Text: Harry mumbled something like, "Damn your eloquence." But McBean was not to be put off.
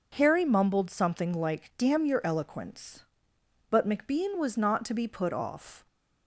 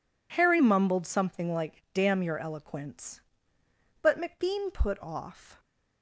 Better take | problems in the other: first | skips "was not to be"; at 4.7 s

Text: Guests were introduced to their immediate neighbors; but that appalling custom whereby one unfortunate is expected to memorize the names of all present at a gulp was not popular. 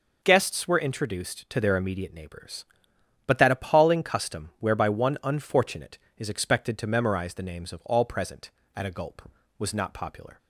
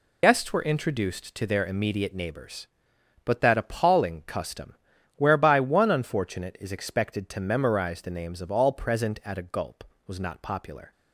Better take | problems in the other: first | loses the start of "Guests"; at 0.2 s; 60 ms // pauses between "custom" and "whereby"; at 4.7 s; 0.44 s long

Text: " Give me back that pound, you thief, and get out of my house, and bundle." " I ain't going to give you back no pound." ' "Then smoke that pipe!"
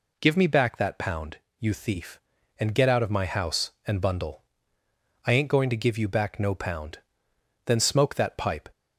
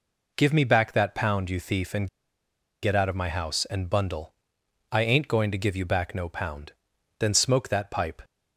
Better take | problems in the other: first | pauses between "and" and "get"; noticeable; at 2.0 s; 0.74 s long

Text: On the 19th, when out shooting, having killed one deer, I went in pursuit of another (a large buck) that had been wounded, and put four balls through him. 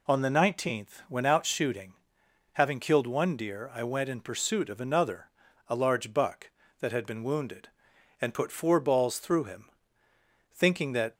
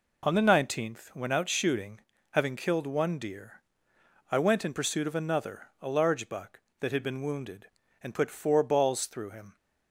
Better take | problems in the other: second | goes on to say "Thinking that"; noticeable; from 10.4 s on; 0.64 s long

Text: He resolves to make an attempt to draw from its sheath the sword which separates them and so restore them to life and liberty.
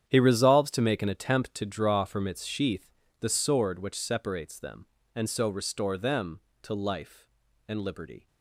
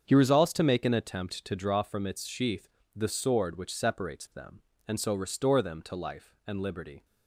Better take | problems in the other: second | gets quieter; strong; throughout; 13.5 dB // starts louder than the rest; strong; until 1.1 s; 9 dB; strong in the second // pauses between "sheath" and "the"; slight; at 2.9 s; 0.28 s long; slight in the second

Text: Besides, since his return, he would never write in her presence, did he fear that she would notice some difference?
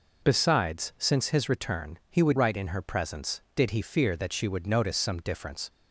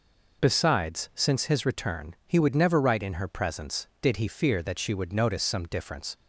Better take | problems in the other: second | skips "never"; at 2.3 s

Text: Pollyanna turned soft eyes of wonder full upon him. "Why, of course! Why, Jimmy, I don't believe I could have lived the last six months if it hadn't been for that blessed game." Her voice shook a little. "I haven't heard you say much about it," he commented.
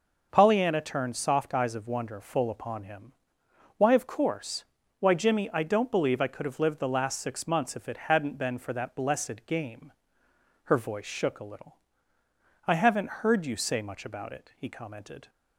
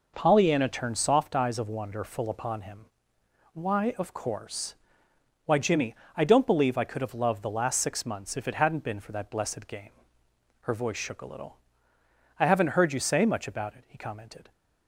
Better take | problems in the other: first | says "loved" for "lived"; at 7.1 s

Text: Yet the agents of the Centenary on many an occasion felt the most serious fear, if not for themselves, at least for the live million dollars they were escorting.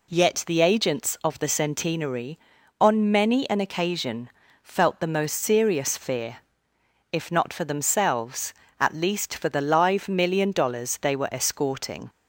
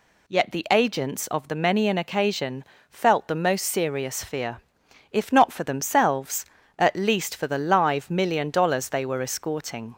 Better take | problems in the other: first | skips "Centenary on"; at 1.5 s // pauses between "occasion" and "felt"; slight; at 2.6 s; 0.26 s long; slight in the first

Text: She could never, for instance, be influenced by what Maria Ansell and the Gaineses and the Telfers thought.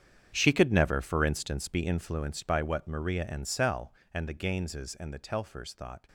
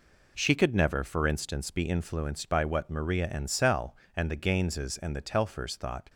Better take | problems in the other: second | gets quieter; strong; throughout; 15.5 dB

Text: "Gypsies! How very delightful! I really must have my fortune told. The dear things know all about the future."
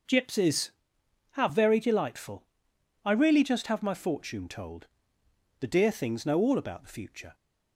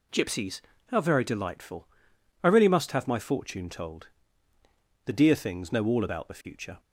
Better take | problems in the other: second | starts louder than the rest; noticeable; until 1.7 s; 6 dB // says "just" for "must"; at 3.4 s

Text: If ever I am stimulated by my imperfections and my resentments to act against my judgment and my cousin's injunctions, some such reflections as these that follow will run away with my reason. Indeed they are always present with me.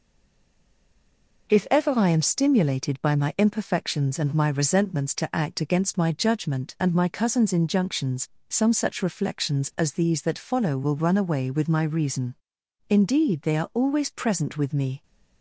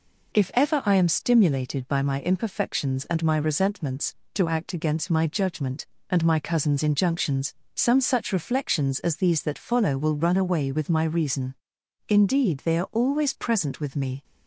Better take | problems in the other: second | stays silent before the first word; noticeable; until 1.4 s; 1.4 s long

